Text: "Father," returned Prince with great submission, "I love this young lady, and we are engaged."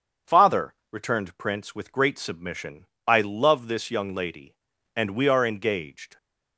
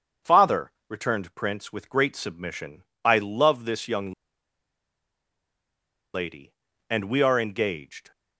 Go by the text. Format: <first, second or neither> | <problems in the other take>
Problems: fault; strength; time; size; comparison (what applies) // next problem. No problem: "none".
first | starts louder than the rest; until 1.4 s; 7 dB; also in the first // pauses between "young" and "lady"; strong; at 4.1 s; 2.0 s long